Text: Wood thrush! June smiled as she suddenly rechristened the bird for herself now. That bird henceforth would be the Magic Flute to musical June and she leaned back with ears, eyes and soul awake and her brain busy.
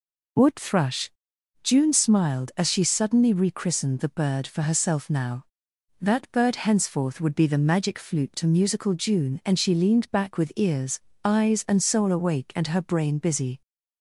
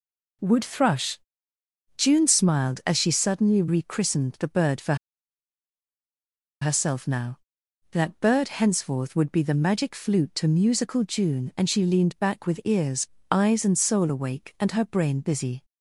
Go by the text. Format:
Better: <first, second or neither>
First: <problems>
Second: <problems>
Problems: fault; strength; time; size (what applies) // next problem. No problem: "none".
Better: first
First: none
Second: pauses between "for" and "herself"; strong; at 4.9 s; 1.6 s long